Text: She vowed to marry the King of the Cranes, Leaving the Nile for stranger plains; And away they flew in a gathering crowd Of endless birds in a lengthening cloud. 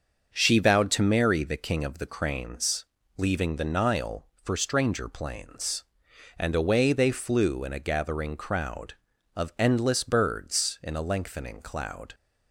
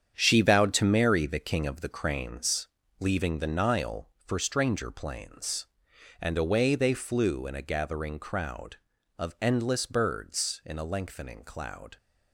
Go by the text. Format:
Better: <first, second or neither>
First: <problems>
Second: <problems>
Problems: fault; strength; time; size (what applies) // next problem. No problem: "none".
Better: first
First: starts louder than the rest; until 1.3 s; 6.5 dB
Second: gets quieter; strong; throughout; 8 dB // starts louder than the rest; strong; until 1.1 s; 8 dB